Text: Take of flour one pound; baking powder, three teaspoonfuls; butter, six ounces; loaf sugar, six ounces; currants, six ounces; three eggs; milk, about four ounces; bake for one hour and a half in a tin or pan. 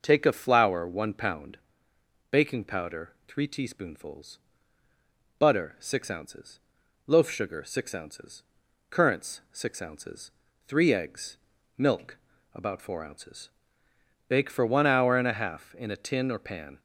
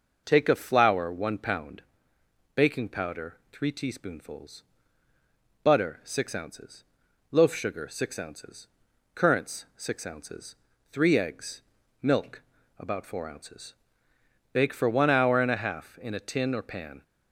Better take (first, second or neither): neither